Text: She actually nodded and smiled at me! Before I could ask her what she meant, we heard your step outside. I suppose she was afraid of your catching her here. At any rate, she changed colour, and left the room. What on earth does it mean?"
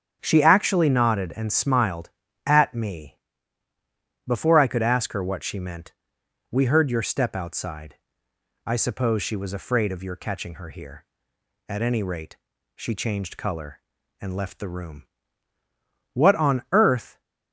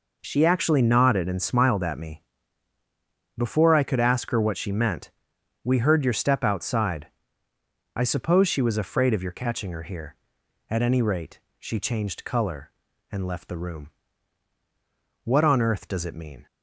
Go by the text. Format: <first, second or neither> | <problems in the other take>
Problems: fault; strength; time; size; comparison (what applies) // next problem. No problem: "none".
second | starts louder than the rest; strong; until 1.2 s; 8.5 dB // stops before "does it mean"; at 17.2 s